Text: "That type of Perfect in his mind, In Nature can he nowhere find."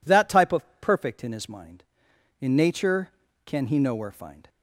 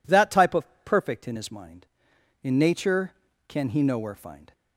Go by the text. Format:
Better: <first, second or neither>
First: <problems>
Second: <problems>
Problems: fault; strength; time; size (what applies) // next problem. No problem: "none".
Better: neither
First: pauses between "of" and "Perfect"; slight; at 0.6 s; 0.16 s long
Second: pauses between "of" and "Perfect"; slight; at 0.6 s; 0.18 s long